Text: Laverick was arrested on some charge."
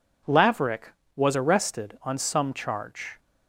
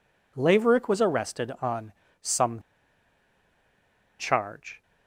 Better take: first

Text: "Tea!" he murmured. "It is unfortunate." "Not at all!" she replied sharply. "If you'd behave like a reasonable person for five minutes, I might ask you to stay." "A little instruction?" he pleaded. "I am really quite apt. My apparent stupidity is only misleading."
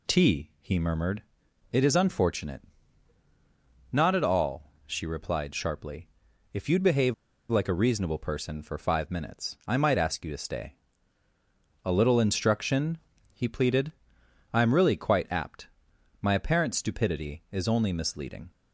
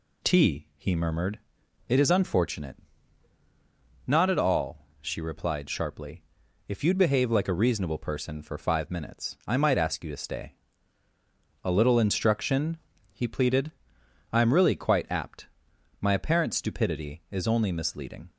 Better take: second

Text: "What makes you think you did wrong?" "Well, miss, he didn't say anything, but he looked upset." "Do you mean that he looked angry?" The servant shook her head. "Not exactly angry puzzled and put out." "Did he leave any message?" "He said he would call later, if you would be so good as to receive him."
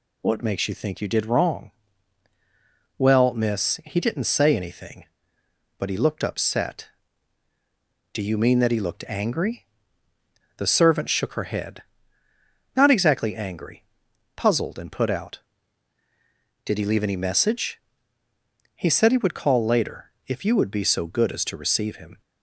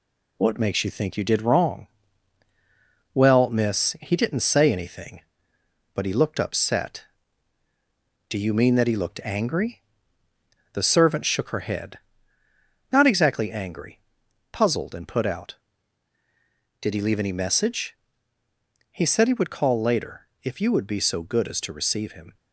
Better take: first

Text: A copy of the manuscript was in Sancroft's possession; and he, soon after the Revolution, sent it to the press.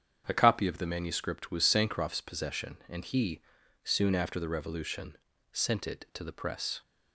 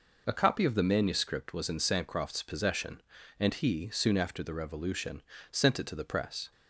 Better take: second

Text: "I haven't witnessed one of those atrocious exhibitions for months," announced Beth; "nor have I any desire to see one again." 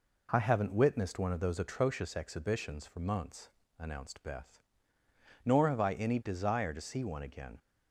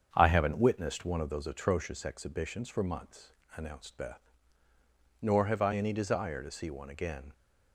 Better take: first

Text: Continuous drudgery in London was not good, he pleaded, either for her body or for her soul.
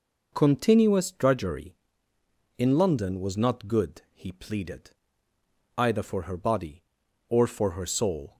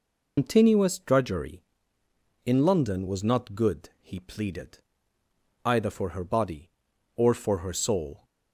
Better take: first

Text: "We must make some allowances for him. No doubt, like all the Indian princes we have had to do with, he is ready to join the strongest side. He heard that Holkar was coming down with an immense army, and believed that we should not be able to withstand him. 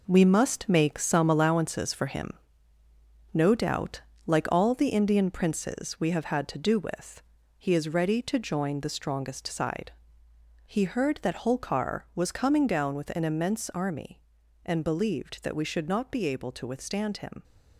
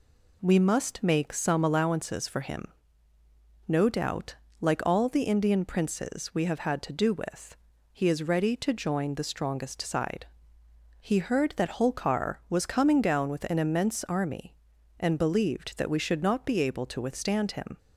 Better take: second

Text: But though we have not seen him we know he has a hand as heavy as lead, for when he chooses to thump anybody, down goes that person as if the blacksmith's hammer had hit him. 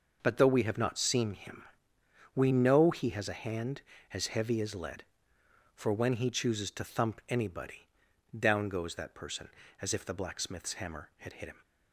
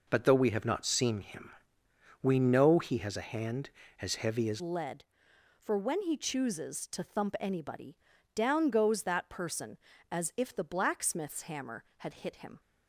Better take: first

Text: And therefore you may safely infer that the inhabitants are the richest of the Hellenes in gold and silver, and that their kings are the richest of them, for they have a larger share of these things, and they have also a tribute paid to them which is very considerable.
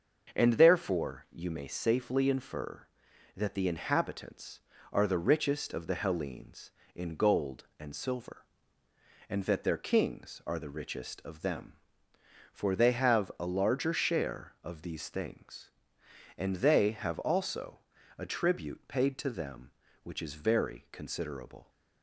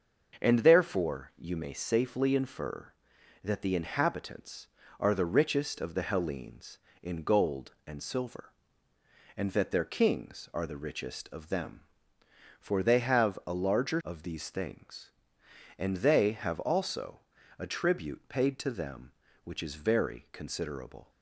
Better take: first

